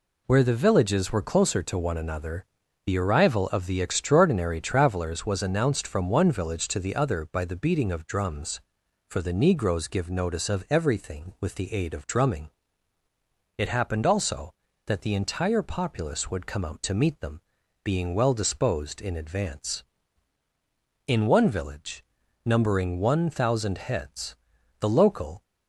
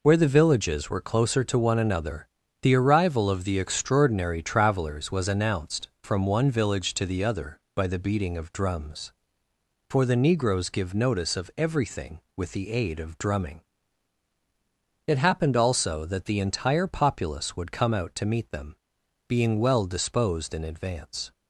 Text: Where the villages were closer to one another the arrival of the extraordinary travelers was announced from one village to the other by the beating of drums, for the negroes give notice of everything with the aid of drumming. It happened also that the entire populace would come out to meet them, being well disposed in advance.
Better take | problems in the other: second | pauses between "another" and "the"; at 2.4 s; 0.42 s long; slight in the second // goes on to say "In one village numbering one thousand heads the local"; strong; from 21.0 s on; 4.3 s long

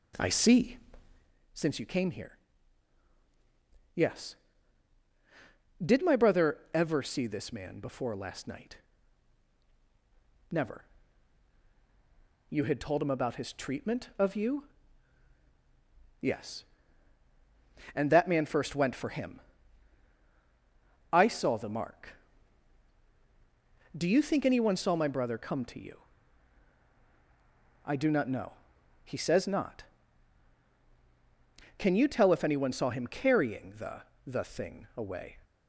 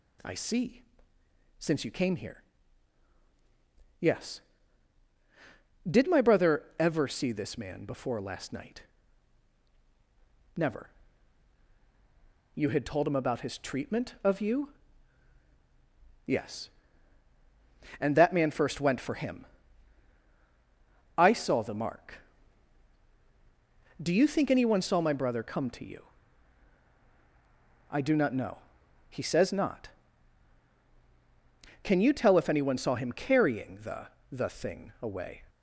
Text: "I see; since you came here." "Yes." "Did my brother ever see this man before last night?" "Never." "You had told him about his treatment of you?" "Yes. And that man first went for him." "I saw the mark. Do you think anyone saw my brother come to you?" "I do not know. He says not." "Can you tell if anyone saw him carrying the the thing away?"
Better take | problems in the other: second | starts louder than the rest; slight; until 1.3 s; 2.5 dB // pauses between "the" and "the"; slight; at 34.0 s; 0.20 s long; slight in the second

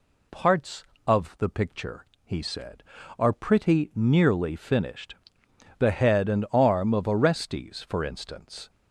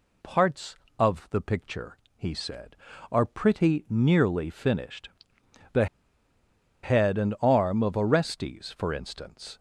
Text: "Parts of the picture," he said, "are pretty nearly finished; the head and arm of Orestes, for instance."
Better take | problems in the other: first | pauses between "the" and "head"; noticeable; at 5.8 s; 0.97 s long

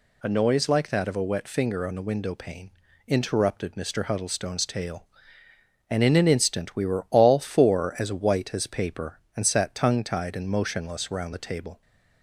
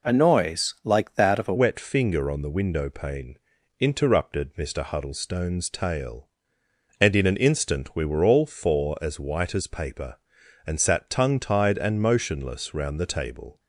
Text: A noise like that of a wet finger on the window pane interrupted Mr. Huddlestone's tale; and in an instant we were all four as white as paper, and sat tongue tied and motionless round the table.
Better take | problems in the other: first | changes voice at "wet"; from 1.5 s on; 12.0 s long // pauses between "pane" and "interrupted"; at 3.3 s; 0.42 s long; slight in the first

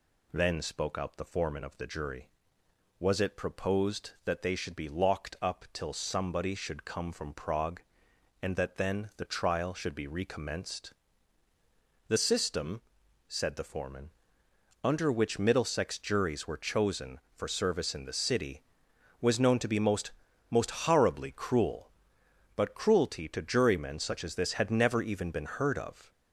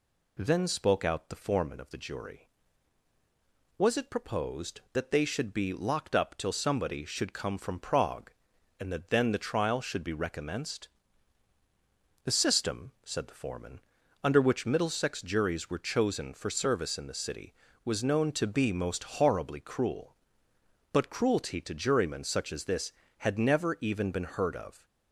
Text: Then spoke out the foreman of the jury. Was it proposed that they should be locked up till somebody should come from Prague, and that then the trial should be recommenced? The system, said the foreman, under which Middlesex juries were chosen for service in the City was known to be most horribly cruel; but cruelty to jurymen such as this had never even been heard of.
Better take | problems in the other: second | says "most" twice; at 20.4 s

